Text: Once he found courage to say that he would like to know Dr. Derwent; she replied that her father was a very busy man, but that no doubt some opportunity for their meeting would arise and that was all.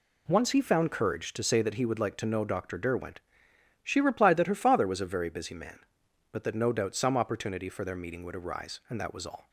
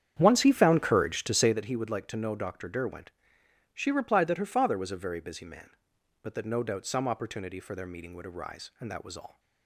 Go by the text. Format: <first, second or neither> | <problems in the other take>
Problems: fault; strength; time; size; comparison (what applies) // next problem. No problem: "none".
first | starts louder than the rest; strong; until 1.6 s; 9 dB